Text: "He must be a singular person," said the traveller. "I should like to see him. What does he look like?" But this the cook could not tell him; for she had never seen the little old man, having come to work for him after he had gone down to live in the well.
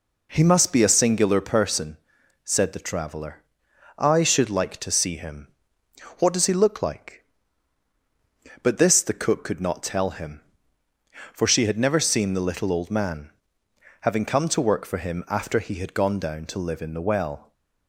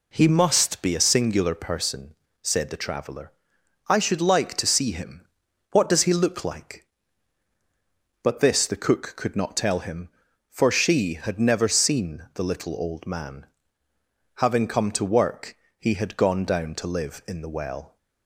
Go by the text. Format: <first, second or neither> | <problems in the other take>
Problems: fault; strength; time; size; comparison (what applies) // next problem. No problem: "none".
first | skips "for him after"; at 15.6 s